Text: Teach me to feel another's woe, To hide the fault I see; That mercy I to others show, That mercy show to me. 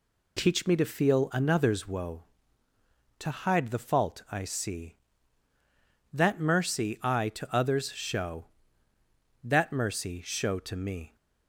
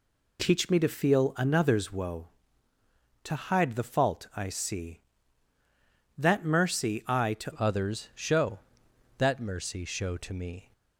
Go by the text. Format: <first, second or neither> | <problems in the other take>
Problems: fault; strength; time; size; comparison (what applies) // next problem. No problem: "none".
first | changes voice at "others"; from 7.5 s on; 3.2 s long